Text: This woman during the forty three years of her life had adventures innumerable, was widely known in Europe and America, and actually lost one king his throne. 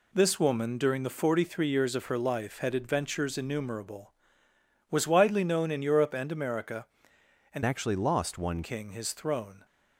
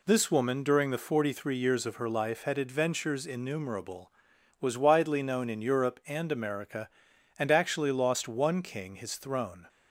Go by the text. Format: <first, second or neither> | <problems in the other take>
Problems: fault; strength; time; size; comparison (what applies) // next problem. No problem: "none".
second | changes voice from "actually" to "one"; from 7.6 to 8.6 s; 1.0 s long